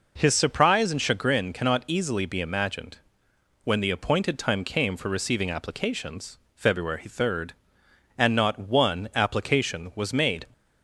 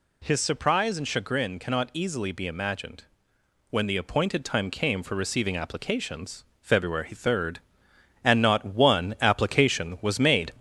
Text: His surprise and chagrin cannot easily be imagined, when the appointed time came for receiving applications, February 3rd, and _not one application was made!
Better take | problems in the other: first | gets louder; slight; throughout; 2.5 dB

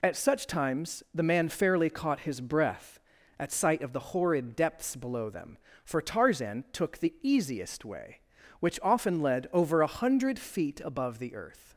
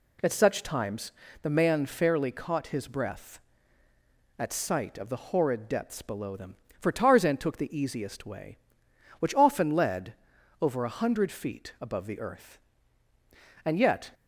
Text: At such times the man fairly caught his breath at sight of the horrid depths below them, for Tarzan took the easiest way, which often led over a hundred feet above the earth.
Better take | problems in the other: first | pauses between "times" and "the"; slight; at 1.1 s; 0.30 s long // pauses between "led" and "over"; noticeable; at 10.1 s; 0.48 s long // goes on to say "And yet"; slight; from 13.6 s on; 0.46 s long

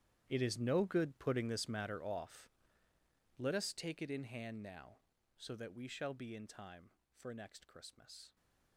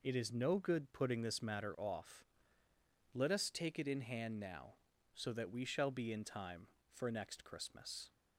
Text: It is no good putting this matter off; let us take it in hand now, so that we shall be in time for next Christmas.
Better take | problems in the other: second | gets quieter; strong; throughout; 16.5 dB

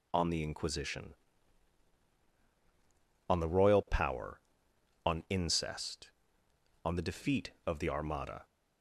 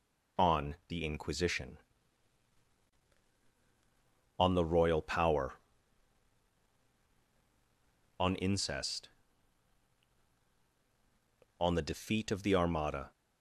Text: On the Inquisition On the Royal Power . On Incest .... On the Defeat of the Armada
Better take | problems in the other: neither | none

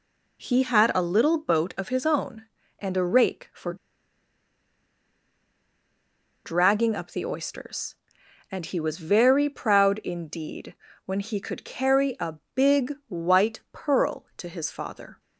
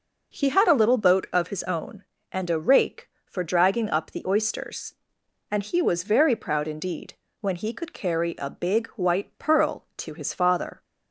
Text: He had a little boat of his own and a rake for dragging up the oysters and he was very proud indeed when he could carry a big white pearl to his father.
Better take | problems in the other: second | pauses between "for" and "dragging"; strong; at 3.7 s; 2.7 s long // pauses between "indeed" and "when"; slight; at 10.7 s; 0.32 s long; slight in the second // pauses between "a" and "big"; slight; at 12.3 s; 0.20 s long // pauses between "big" and "white"; slight; at 12.9 s; 0.16 s long

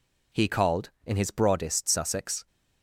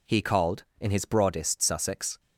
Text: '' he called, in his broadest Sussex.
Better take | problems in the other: neither | none

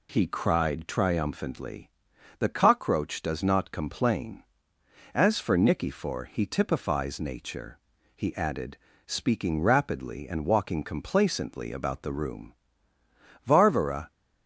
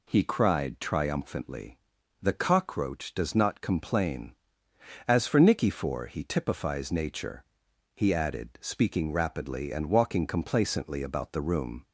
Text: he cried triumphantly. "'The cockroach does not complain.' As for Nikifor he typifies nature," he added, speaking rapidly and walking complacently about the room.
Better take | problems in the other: second | goes on to say "Varvara"; noticeable; from 13.4 s on; 0.66 s long

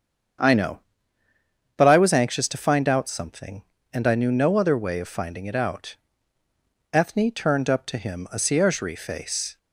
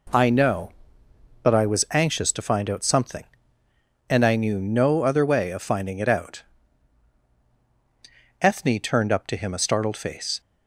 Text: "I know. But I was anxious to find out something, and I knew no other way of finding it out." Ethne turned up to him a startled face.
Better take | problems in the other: second | starts louder than the rest; strong; until 2.3 s; 7.5 dB // says "ciergerie" for "startled"; at 8.3 s

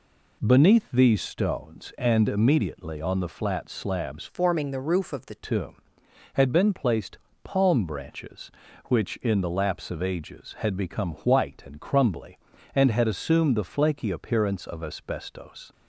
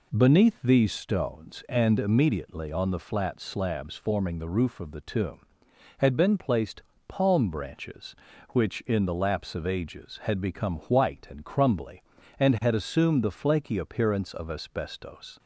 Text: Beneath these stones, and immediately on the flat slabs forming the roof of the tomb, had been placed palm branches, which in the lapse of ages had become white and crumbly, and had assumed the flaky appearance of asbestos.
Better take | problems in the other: second | changes voice from "forming" to "the"; from 4.2 to 5.3 s; 1.1 s long // pauses between "placed" and "palm"; slight; at 7.1 s; 0.26 s long; slight in the second

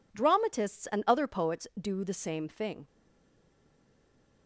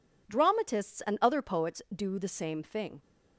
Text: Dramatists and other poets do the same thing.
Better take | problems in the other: second | stays silent after the last word; noticeable; from 2.8 s on; 1.6 s long

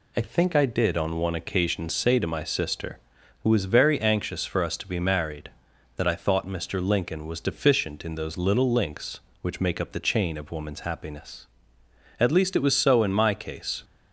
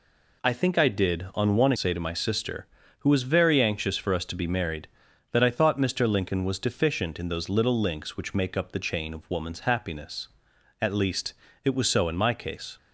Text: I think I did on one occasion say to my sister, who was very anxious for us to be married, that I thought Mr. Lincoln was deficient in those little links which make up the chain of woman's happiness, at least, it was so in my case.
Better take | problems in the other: first | skips "occasion"; at 1.7 s

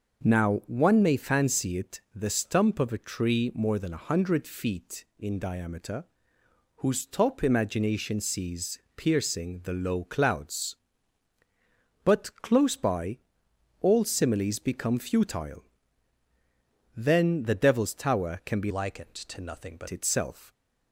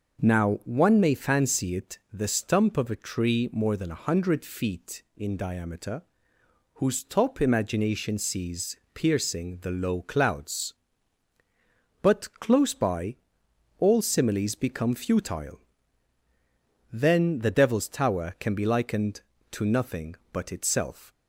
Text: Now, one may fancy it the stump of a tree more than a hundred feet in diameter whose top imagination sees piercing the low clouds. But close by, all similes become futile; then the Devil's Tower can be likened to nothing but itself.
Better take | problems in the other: second | pauses between "diameter" and "whose"; noticeable; at 6.0 s; 0.72 s long; noticeable in the second // pauses between "sees" and "piercing"; slight; at 8.7 s; 0.18 s long; slight in the second // changes voice from "likened" to "but"; from 18.7 to 19.8 s; 1.1 s long

